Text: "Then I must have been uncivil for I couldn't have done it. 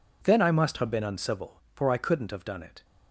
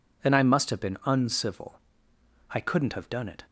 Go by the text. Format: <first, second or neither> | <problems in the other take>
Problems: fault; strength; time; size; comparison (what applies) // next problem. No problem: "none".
first | skips "for"; at 2.1 s